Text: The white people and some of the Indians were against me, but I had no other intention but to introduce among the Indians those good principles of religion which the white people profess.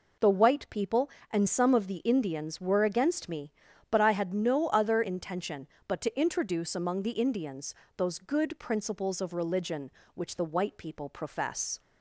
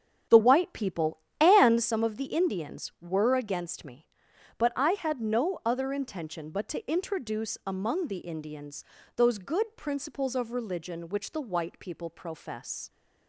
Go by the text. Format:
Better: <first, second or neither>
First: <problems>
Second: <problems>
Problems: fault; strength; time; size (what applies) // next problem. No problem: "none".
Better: first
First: pauses between "Indians" and "those"; slight; at 7.7 s; 0.24 s long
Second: starts louder than the rest; strong; until 2.0 s; 8.5 dB // pauses between "Indians" and "those"; slight; at 8.8 s; 0.34 s long